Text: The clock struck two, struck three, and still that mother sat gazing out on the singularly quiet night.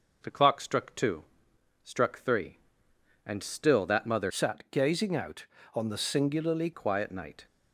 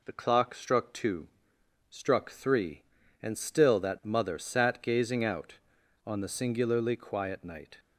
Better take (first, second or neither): second